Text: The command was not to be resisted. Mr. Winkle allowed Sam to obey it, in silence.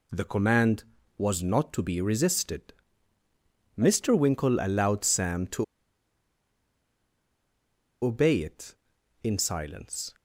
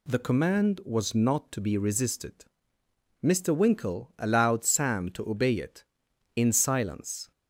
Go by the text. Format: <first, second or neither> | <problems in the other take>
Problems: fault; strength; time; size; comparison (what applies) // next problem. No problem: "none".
second | pauses between "to" and "obey"; strong; at 5.6 s; 2.4 s long